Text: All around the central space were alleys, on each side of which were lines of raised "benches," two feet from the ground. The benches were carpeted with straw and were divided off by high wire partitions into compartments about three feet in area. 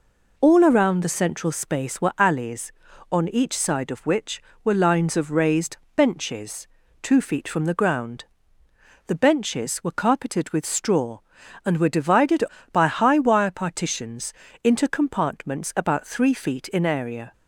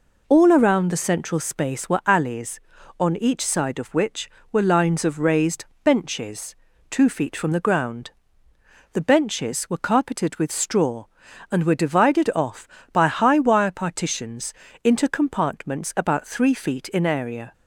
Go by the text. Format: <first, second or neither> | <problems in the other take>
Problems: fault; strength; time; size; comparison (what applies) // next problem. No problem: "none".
second | pauses between "raised" and "benches"; slight; at 5.7 s; 0.18 s long; slight in the second // skips "off"; at 12.5 s // pauses between "partitions" and "into"; slight; at 14.3 s; 0.32 s long; slight in the second